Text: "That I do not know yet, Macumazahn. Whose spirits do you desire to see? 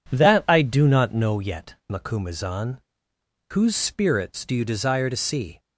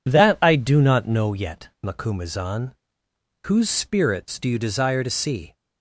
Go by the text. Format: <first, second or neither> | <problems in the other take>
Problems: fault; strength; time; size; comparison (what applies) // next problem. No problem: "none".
first | loses the start of "That"; at 0.0 s; 65 ms